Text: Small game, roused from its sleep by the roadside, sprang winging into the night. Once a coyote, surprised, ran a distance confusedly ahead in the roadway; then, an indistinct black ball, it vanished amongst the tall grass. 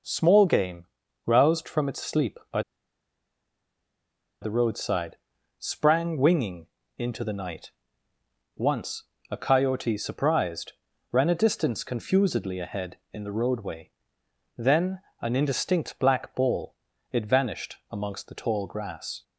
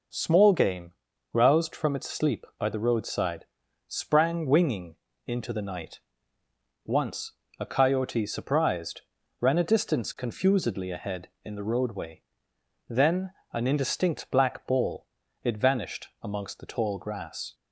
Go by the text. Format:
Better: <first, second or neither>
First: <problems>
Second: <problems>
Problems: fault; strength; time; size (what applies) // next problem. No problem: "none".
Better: second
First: pauses between "by" and "the"; strong; at 2.6 s; 1.8 s long // pauses between "winging" and "into"; slight; at 6.6 s; 0.30 s long // pauses between "Once" and "a"; slight; at 9.0 s; 0.26 s long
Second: pauses between "winging" and "into"; slight; at 4.9 s; 0.30 s long // pauses between "Once" and "a"; slight; at 7.3 s; 0.26 s long